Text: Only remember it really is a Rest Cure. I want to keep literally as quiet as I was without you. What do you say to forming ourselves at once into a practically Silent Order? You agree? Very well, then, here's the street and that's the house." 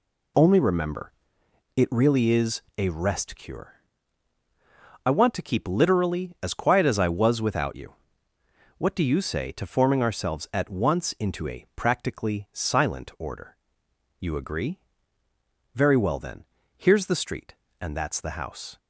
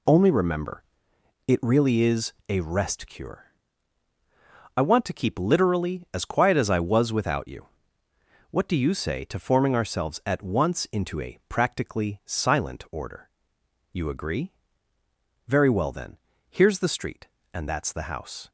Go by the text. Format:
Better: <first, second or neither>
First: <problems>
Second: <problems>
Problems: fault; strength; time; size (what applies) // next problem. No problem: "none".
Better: neither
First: pauses between "remember" and "it"; noticeable; at 1.1 s; 0.66 s long // pauses between "is" and "a"; slight; at 2.6 s; 0.18 s long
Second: pauses between "remember" and "it"; noticeable; at 0.8 s; 0.66 s long // pauses between "is" and "a"; slight; at 2.3 s; 0.18 s long